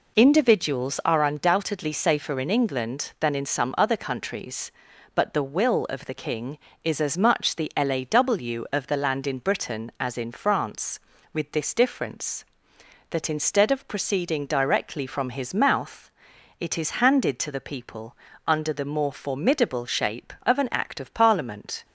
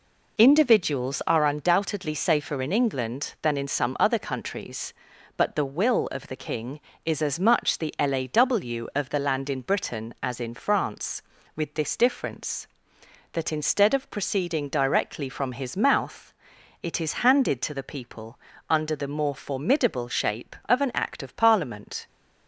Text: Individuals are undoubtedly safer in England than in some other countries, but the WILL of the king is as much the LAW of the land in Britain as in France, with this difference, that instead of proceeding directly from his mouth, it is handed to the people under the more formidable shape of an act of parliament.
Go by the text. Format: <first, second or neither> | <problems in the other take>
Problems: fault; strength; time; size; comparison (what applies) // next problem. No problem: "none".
neither | pauses between "people" and "under"; slight; the same in both